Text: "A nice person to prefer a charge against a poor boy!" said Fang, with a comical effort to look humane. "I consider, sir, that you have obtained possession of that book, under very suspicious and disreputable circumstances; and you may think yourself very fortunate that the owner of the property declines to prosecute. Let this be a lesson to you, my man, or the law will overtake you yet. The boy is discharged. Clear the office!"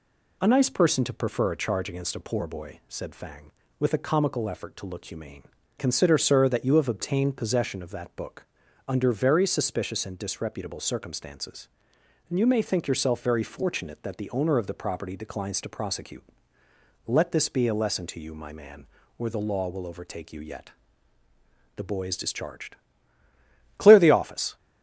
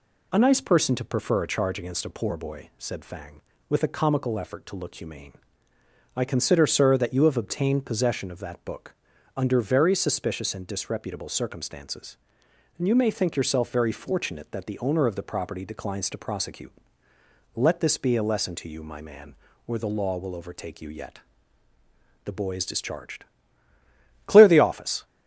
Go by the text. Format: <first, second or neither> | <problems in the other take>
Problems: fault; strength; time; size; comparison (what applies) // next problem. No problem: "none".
second | skips "I"; at 5.6 s